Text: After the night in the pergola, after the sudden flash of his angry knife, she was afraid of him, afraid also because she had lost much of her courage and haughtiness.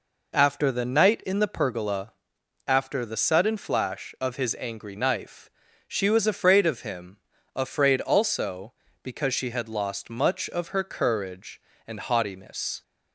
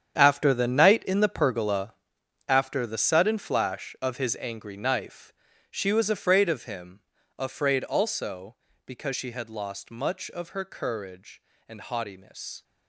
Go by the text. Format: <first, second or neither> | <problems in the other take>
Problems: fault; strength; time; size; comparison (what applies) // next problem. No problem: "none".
first | gets quieter; strong; throughout; 13.5 dB